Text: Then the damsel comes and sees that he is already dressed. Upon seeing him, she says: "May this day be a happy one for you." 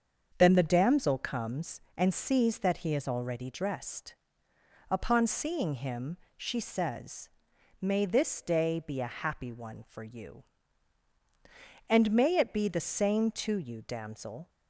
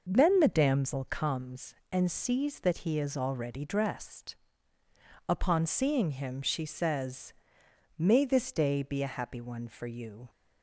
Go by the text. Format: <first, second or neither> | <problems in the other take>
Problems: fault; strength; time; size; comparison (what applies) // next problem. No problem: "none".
second | starts louder than the rest; until 1.3 s; 7 dB // goes on to say "And may it be the same to you damsel"; strong; from 11.8 s on; 2.6 s long